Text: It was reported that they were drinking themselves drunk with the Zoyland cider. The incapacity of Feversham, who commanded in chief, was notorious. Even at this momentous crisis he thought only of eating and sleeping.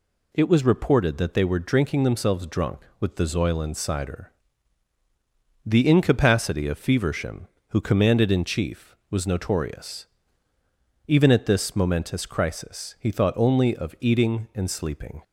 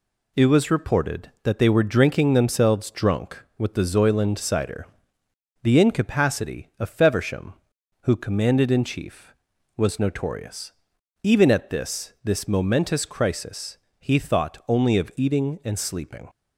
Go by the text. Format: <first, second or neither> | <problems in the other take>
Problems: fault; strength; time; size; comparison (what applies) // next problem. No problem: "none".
first | says "this" twice; at 12.2 s // pauses between "crisis" and "he"; slight; at 13.7 s; 0.22 s long